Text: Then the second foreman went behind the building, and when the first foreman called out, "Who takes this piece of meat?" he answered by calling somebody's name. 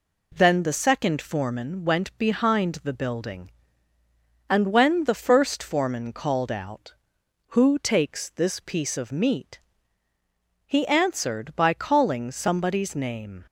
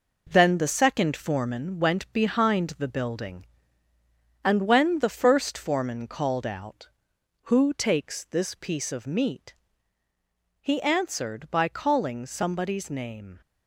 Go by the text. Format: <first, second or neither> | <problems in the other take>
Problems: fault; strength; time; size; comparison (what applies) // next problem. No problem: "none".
first | gets quieter; strong; throughout; 7 dB